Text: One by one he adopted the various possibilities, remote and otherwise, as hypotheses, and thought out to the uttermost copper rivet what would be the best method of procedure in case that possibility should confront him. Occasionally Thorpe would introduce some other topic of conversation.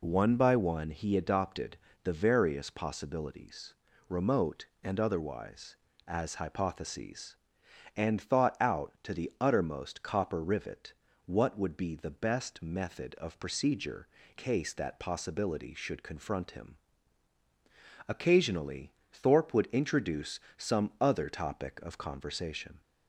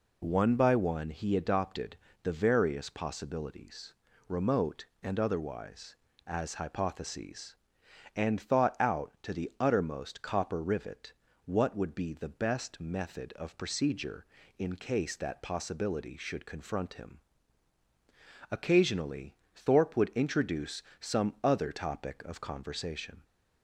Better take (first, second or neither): second